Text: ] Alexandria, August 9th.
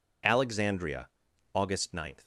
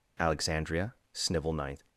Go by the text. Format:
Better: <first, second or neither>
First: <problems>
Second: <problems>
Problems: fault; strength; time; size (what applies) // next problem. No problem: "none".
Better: first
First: none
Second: says "Snivel" for "August"; at 1.1 s